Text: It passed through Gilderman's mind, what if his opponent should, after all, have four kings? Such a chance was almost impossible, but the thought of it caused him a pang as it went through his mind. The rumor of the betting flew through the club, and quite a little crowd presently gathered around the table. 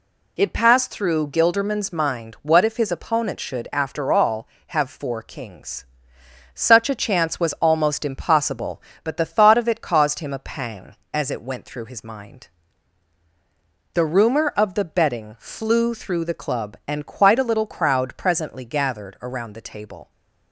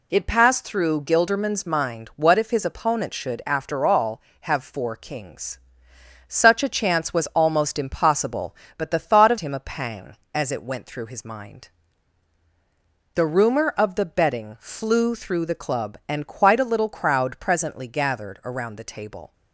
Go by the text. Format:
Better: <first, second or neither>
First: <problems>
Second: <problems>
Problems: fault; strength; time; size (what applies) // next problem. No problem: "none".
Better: first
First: none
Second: skips "it caused"; at 9.3 s